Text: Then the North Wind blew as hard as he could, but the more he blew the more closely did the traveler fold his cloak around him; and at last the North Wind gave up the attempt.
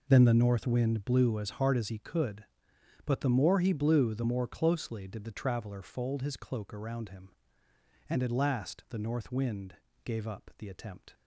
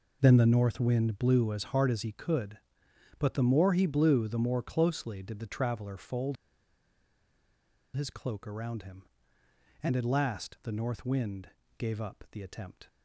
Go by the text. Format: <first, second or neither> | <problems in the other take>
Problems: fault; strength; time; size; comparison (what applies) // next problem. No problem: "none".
first | pauses between "fold" and "his"; strong; at 6.3 s; 1.6 s long // pauses between "Wind" and "gave"; slight; at 11.4 s; 0.28 s long; slight in the first